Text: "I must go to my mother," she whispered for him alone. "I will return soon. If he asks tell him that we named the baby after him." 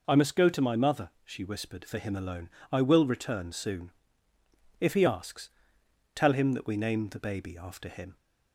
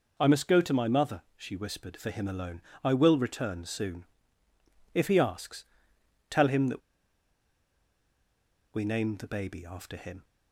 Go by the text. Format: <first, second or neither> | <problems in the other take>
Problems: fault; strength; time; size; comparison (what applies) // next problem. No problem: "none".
first | pauses between "asks" and "tell"; noticeable; at 5.6 s; 0.64 s long; noticeable in the first // pauses between "that" and "we"; strong; at 6.8 s; 1.9 s long